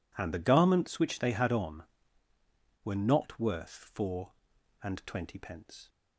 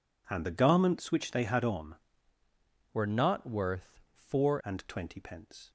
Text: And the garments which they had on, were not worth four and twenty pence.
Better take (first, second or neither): first